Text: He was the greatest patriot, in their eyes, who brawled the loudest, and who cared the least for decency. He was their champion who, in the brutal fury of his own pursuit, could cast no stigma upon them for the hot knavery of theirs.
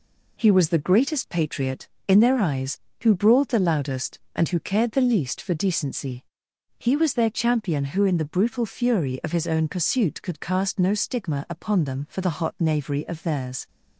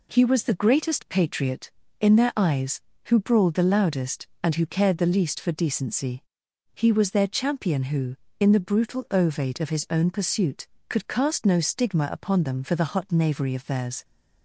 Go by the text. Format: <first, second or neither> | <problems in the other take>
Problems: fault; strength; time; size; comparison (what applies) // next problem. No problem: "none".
first | says "ovate" for "fury"; at 9.1 s